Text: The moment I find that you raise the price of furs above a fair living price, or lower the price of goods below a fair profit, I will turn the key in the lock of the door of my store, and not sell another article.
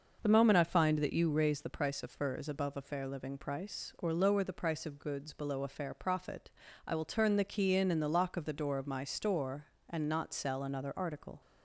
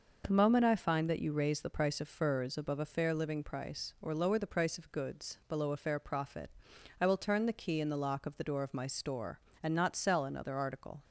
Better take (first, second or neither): second